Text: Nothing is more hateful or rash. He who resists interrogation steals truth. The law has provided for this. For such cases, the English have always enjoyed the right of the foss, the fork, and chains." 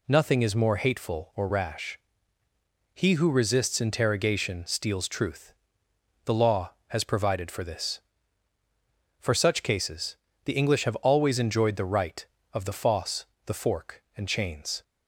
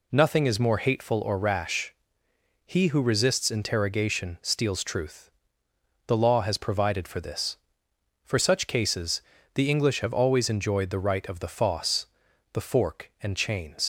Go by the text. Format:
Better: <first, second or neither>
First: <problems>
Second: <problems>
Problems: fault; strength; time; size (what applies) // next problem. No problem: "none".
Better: first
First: none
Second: leaves "chains" unfinished; at 13.8 s; 95 ms